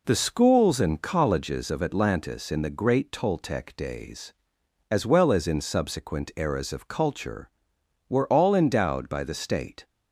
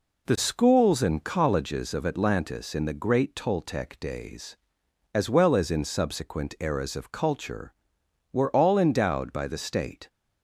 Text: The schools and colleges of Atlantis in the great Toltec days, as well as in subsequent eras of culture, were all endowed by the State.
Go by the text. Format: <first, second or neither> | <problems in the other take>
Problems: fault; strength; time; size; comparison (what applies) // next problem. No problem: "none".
neither | none